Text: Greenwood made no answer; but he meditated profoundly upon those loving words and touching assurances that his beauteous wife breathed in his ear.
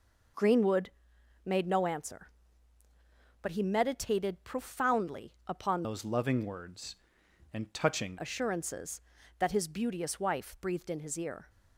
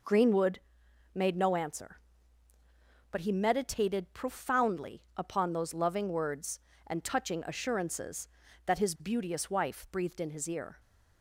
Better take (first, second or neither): second